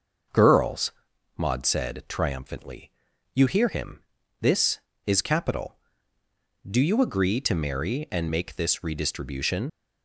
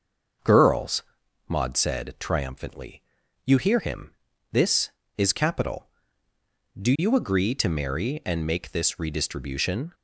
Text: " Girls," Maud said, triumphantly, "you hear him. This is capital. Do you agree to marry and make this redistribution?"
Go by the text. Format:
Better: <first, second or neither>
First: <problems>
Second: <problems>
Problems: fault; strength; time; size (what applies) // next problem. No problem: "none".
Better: second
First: starts louder than the rest; until 1.7 s; 6.5 dB // leaves "redistribution" unfinished; at 9.6 s; 85 ms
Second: starts louder than the rest; until 1.9 s; 6.5 dB